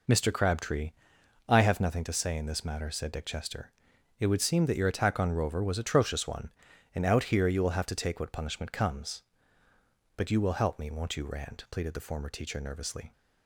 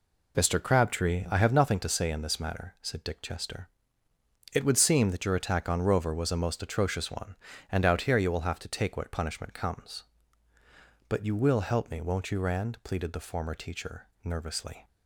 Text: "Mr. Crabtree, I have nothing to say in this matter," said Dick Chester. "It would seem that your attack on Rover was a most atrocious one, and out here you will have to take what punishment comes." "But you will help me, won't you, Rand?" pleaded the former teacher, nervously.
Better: second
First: skips "a most"; at 5.7 s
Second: none

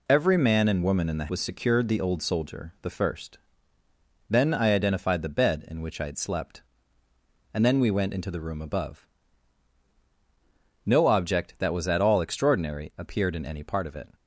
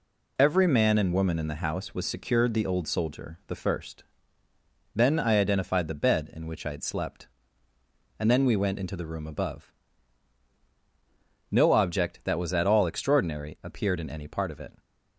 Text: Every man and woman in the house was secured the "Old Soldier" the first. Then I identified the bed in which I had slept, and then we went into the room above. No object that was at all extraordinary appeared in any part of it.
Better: second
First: skips "house"; at 1.2 s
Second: none

